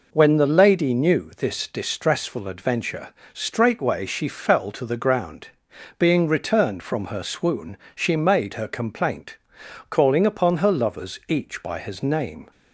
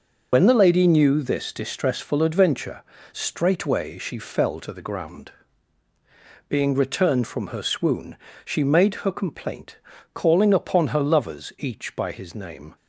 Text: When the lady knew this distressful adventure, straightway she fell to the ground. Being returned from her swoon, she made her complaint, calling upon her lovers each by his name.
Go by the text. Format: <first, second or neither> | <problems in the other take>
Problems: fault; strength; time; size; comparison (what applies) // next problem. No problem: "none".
first | loses the start of "When"; at 0.3 s; 55 ms